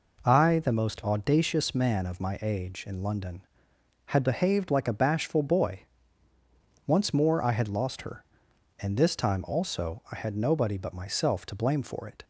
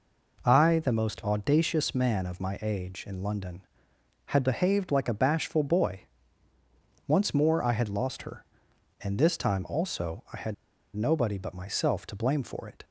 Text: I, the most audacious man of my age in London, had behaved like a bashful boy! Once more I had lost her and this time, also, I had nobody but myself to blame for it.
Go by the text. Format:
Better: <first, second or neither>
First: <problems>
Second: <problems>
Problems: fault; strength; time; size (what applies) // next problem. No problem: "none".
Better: first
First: none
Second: pauses between "had" and "nobody"; at 10.5 s; 0.41 s long